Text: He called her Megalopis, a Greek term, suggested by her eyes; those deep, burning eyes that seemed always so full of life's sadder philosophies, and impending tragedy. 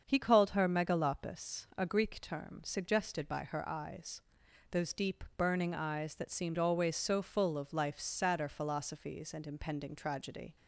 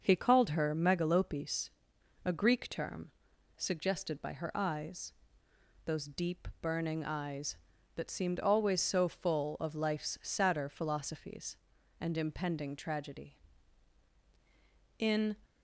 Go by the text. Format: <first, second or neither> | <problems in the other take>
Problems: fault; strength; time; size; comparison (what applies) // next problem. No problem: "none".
first | starts louder than the rest; until 1.0 s; 6.5 dB; also in the first // goes on to say "In"; slight; from 14.9 s on; 0.38 s long